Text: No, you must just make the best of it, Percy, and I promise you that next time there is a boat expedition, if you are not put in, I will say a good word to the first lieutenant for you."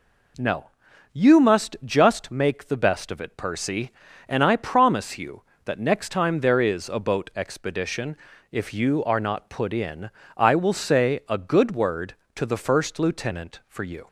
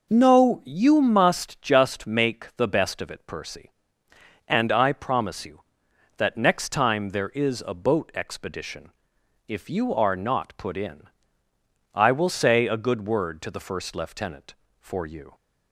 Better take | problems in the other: neither | none

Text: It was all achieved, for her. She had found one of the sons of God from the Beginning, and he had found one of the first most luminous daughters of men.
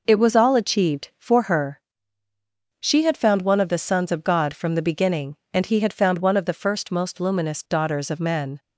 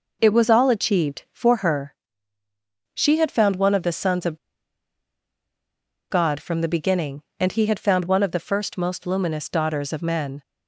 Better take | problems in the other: first | pauses between "of" and "God"; strong; at 4.3 s; 1.7 s long

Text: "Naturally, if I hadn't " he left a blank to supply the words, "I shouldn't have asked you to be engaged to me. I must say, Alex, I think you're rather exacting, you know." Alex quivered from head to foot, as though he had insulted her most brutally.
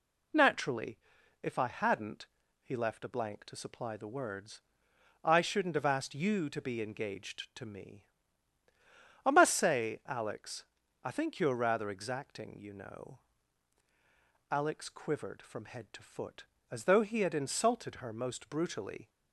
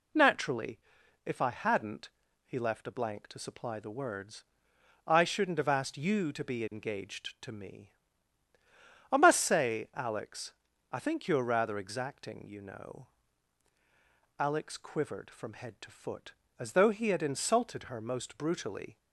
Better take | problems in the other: neither | none

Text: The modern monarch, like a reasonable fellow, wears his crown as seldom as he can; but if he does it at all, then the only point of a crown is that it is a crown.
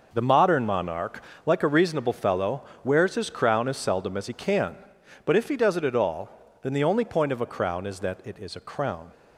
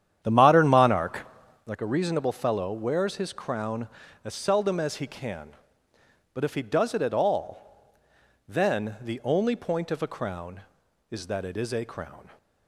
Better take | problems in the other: first | starts louder than the rest; strong; until 1.8 s; 10 dB

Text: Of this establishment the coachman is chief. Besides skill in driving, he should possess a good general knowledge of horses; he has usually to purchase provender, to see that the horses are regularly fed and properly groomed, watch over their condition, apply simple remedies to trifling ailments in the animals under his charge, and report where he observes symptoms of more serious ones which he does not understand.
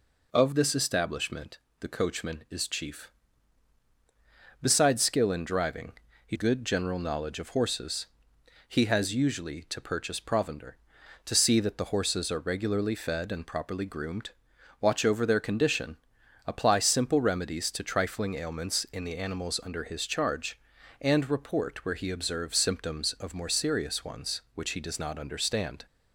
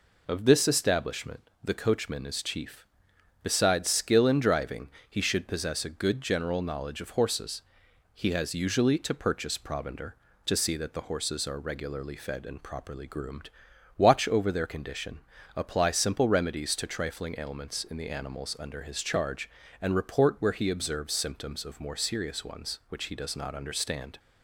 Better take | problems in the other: second | pauses between "establishment" and "the"; slight; at 1.5 s; 0.22 s long // skips "should possess a"; at 6.3 s

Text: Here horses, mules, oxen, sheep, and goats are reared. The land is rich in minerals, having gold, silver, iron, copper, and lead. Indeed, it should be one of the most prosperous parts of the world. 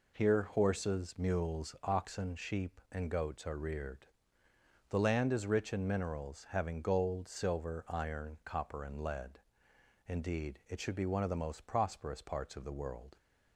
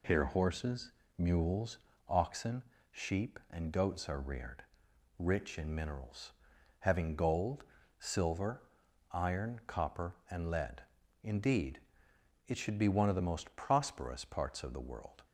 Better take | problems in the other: first | skips "The land is"; at 4.8 s

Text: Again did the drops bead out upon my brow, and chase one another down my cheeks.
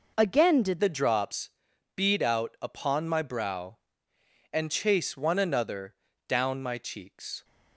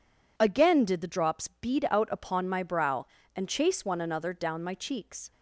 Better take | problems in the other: second | changes voice at "the"; from 0.8 s on; 6.6 s long // pauses between "drops" and "bead"; at 1.5 s; 0.44 s long // pauses between "another" and "down"; slight; at 5.9 s; 0.32 s long

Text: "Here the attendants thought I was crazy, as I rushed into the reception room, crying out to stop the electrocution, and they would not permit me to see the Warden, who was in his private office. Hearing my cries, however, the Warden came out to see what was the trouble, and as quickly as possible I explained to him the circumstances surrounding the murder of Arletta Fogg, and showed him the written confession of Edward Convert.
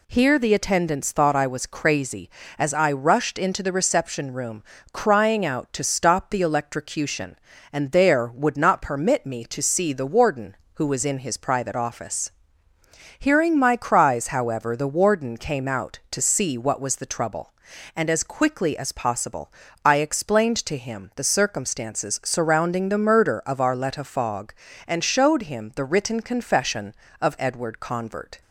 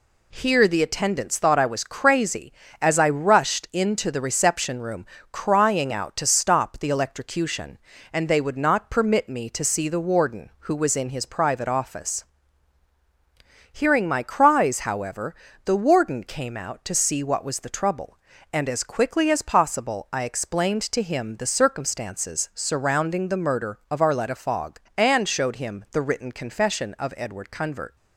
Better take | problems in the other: second | says "there" for "they"; at 7.9 s // pauses between "possible" and "I"; slight; at 19.5 s; 0.32 s long

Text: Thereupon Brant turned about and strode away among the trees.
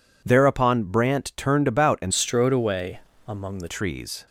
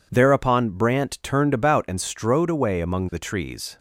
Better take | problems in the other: second | changes voice from "strode" to "the"; from 2.1 to 3.6 s; 1.5 s long // pauses between "away" and "among"; slight; at 3.0 s; 0.26 s long

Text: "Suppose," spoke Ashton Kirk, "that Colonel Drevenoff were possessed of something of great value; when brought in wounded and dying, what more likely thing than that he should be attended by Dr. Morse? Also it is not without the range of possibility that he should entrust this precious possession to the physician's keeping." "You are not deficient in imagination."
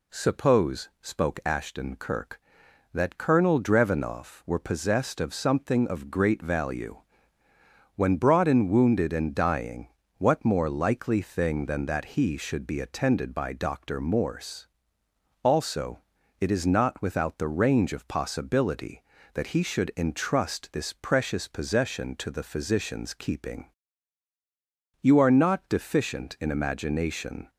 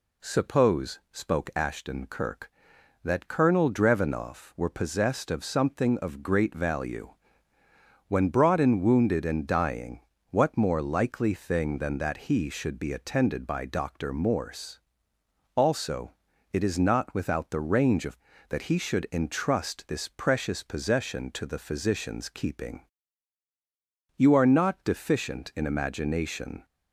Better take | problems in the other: first | pauses between "Also" and "it"; at 16.1 s; 0.40 s long; also in the first // skips "possibility"; at 18.3 s

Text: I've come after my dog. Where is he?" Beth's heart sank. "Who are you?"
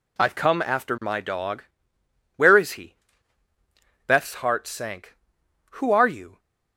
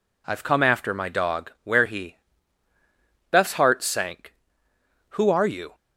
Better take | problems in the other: first | skips "is"; at 1.8 s

